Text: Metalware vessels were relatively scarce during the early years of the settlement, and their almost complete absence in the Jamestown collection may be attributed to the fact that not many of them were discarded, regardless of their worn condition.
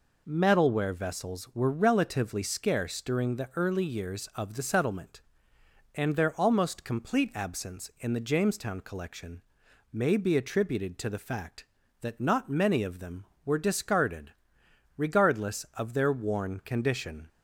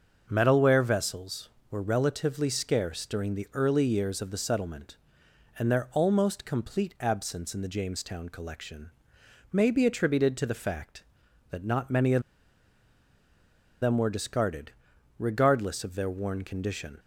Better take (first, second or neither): first